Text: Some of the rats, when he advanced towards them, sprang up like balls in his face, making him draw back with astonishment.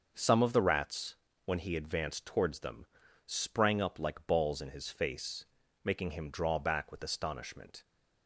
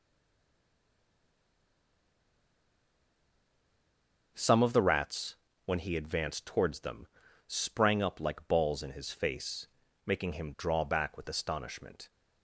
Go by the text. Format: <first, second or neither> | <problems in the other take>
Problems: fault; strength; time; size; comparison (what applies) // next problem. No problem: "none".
first | stays silent before the first word; strong; until 4.3 s; 4.3 s long // starts louder than the rest; until 5.3 s; 6 dB; also in the first